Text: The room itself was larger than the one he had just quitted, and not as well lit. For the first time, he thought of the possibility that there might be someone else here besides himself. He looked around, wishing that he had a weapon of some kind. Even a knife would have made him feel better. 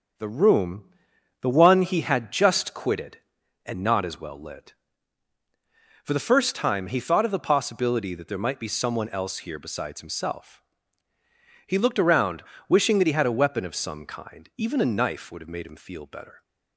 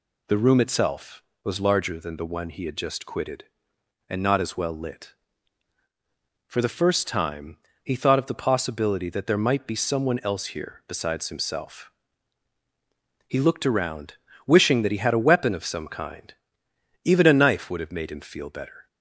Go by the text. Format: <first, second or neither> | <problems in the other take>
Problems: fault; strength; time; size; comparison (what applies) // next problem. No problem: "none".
second | starts louder than the rest; until 1.7 s; 6.5 dB // skips "itself was larger than"; at 1.1 s